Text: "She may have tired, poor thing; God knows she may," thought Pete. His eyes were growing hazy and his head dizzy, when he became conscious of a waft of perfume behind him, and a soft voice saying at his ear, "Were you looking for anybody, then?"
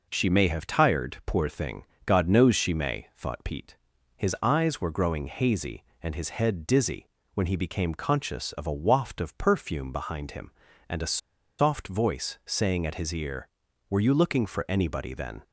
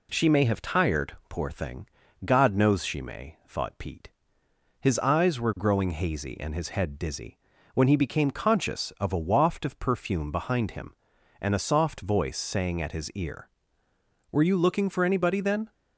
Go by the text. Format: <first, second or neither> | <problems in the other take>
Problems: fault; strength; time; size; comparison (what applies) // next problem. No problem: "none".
second | pauses between "a" and "soft"; at 11.1 s; 0.41 s long